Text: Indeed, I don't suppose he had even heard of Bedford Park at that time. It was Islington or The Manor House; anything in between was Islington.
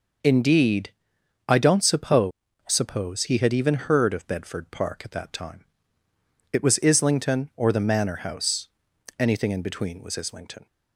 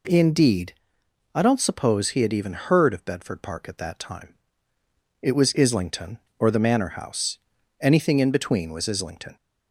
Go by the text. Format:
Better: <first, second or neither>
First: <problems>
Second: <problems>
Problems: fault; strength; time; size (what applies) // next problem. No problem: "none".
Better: second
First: says "suppose" twice; at 2.6 s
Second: none